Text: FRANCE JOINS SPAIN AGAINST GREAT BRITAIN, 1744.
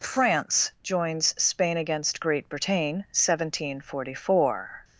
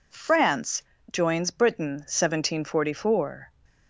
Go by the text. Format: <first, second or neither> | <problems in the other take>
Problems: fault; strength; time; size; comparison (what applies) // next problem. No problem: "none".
first | pauses between "FRANCE" and "JOINS"; slight; at 0.8 s; 0.28 s long // skips "SPAIN AGAINST GREAT"; at 1.5 s